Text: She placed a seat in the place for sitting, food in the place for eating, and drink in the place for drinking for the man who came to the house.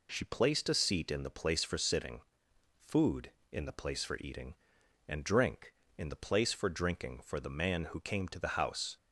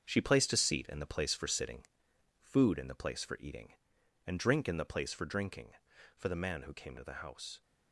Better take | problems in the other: first | gets quieter; strong; throughout; 8.5 dB

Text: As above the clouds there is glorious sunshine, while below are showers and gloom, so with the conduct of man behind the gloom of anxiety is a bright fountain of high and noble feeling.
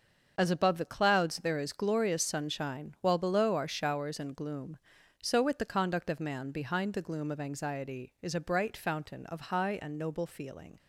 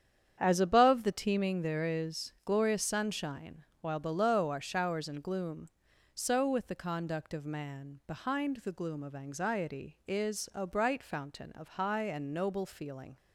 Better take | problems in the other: first | starts louder than the rest; strong; until 1.4 s; 8.5 dB; also in the first // says "teeming" for "clouds"; at 1.1 s

